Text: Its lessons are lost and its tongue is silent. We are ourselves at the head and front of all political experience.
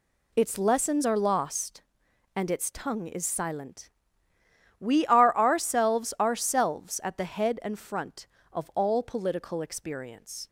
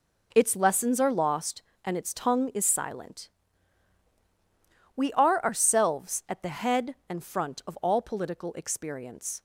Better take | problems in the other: second | says "ourselves" twice; at 6.1 s

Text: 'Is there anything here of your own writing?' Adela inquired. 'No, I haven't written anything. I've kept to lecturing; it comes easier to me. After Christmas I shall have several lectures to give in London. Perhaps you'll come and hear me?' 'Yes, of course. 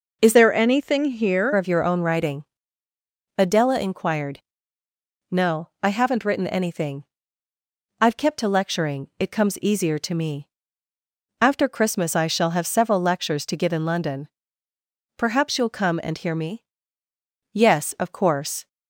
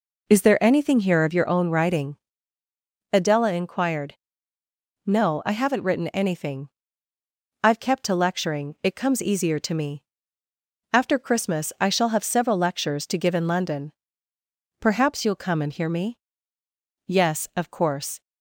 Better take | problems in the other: second | changes voice from "there" to "here"; from 0.3 to 1.5 s; 1.2 s long

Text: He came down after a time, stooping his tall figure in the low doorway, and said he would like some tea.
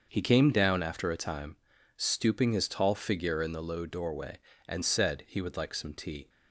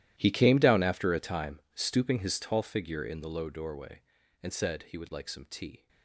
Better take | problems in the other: first | gets quieter; strong; throughout; 20 dB // starts louder than the rest; strong; until 1.1 s; 13 dB; also in the first

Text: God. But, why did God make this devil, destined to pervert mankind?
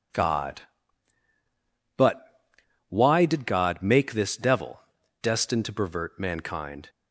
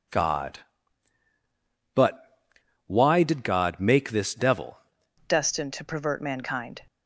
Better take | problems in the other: first | changes voice at "destined"; from 5.2 s on; 1.6 s long

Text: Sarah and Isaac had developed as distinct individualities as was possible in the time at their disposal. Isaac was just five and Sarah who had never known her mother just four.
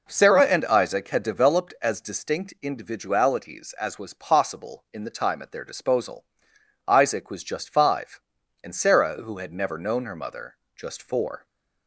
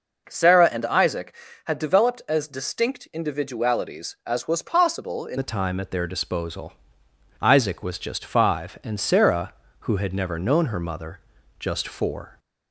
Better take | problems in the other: first | changes voice at "the"; from 5.3 s on; 7.0 s long // pauses between "mother" and "just"; at 11.1 s; 0.40 s long; slight in the first

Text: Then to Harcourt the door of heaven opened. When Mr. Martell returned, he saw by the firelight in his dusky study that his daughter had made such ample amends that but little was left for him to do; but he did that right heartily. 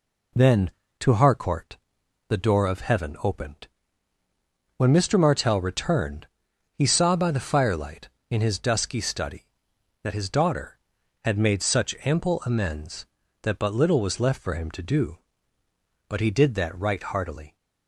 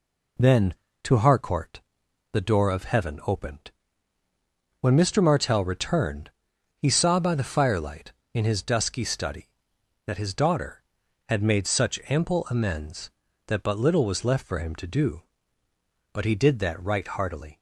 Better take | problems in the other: neither | pauses between "Harcourt" and "the"; noticeable; the same in both

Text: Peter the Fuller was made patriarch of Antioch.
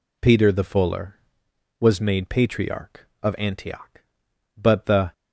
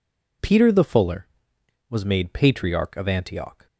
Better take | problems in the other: second | goes on to say "But the"; from 4.5 s on; 0.56 s long

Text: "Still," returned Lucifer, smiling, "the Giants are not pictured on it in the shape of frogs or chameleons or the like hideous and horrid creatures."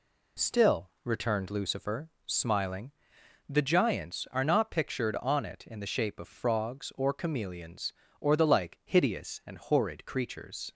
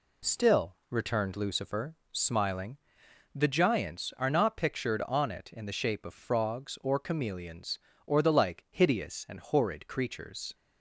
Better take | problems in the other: neither | none

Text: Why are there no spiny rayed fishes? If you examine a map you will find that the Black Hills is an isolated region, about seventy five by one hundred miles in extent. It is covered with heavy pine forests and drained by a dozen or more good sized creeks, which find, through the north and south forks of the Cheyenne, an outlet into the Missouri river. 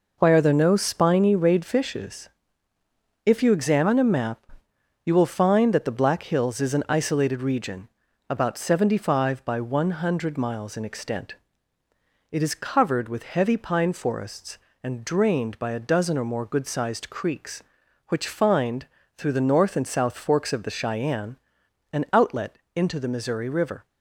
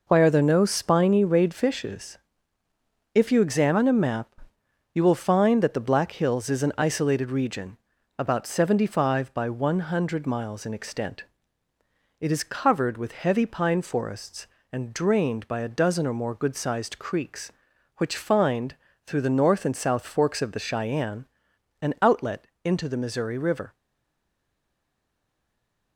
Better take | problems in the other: first | pauses between "map" and "you"; noticeable; at 4.3 s; 0.60 s long; noticeable in the first // pauses between "outlet" and "into"; slight; at 22.4 s; 0.18 s long; slight in the first // stays silent after the last word; from 23.7 s on; 2.2 s long

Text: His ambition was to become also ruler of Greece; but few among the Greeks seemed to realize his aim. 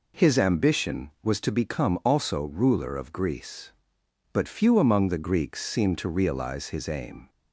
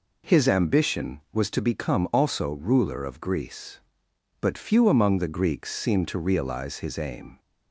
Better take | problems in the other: neither | none

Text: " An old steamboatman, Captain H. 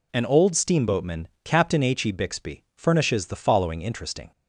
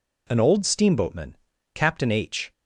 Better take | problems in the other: second | goes on to say "E Bixby furnishes the following interesting"; strong; from 2.0 s on; 2.2 s long

